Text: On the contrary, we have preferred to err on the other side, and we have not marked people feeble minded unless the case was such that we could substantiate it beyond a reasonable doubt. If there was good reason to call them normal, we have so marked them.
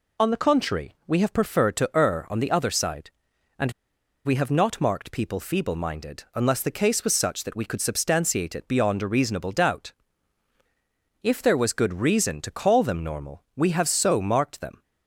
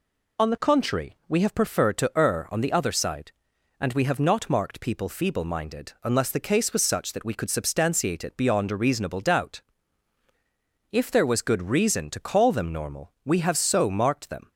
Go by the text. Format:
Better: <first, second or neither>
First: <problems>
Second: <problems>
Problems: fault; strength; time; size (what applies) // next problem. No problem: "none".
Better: second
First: pauses between "and" and "we"; noticeable; at 3.7 s; 0.53 s long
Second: none